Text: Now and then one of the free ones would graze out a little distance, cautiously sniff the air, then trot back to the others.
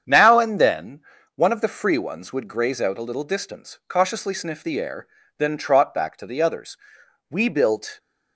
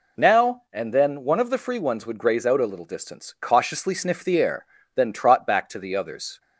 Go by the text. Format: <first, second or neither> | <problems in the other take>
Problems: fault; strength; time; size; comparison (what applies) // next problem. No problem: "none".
second | starts louder than the rest; strong; until 1.4 s; 8 dB // pauses between "then" and "one"; slight; at 1.0 s; 0.34 s long // goes on to say "We built"; noticeable; from 7.3 s on; 0.68 s long